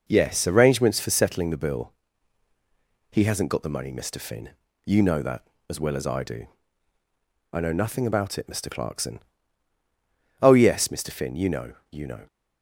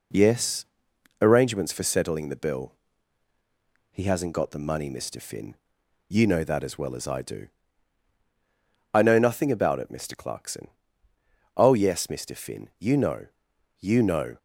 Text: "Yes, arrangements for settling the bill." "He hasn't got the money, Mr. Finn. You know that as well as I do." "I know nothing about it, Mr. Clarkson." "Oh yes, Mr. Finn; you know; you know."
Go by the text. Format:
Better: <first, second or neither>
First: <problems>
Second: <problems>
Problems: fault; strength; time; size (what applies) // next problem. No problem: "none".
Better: neither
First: none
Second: none